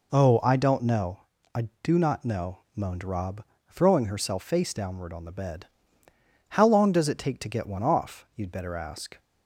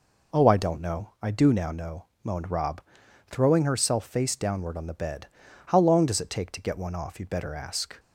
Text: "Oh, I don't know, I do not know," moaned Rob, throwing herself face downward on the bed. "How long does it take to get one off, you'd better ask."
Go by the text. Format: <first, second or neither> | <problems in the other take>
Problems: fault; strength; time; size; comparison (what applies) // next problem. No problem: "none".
first | says "now" for "not"; at 1.5 s